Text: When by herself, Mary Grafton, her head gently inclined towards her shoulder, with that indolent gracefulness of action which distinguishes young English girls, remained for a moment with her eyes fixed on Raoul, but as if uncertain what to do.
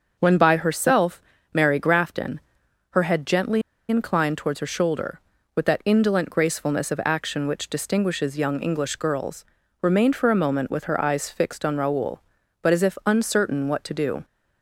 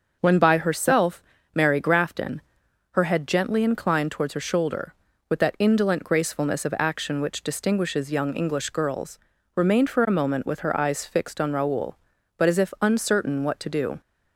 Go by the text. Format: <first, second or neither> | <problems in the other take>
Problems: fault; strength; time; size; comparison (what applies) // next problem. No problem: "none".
second | starts louder than the rest; until 1.2 s; 6 dB; also in the second // pauses between "gently" and "inclined"; slight; at 3.6 s; 0.27 s long